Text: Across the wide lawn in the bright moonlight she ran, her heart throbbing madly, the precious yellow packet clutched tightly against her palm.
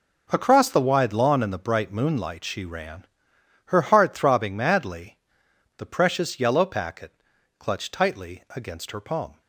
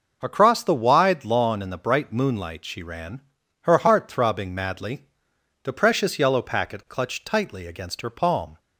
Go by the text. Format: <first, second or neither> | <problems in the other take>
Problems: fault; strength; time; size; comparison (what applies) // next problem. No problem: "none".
second | gets quieter; strong; throughout; 12.5 dB // pauses between "packet" and "clutched"; noticeable; at 7.1 s; 0.46 s long